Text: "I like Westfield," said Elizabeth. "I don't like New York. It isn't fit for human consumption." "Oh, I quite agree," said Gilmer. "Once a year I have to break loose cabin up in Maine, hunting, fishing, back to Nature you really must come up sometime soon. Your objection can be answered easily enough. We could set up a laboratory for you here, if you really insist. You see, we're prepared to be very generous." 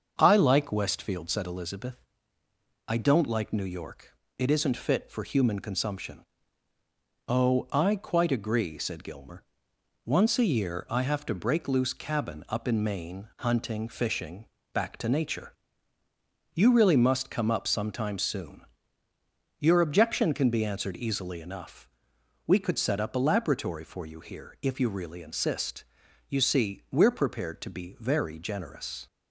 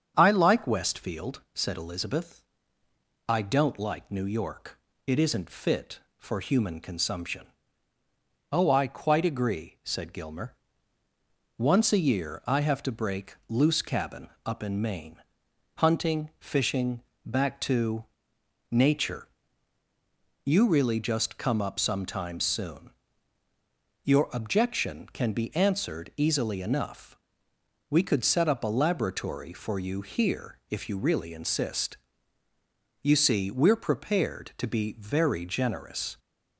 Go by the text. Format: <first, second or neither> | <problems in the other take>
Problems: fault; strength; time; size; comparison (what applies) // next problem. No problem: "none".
first | starts louder than the rest; strong; until 1.1 s; 7.5 dB; also in the first // pauses between "cabin" and "up"; slight; at 14.2 s; 0.18 s long // pauses between "to" and "Nature"; noticeable; at 18.0 s; 0.66 s long // pauses between "Nature" and "you"; at 19.2 s; 1.1 s long; also in the first // says "just" for "must"; at 21.0 s